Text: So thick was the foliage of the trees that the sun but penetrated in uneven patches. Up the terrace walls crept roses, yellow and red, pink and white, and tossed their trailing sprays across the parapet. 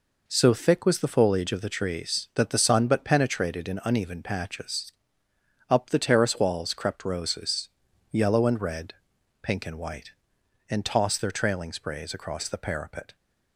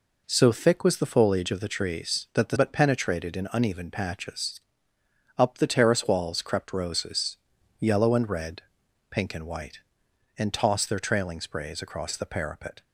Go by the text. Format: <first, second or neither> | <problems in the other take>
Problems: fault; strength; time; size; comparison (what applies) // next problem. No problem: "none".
first | skips "sun"; at 2.5 s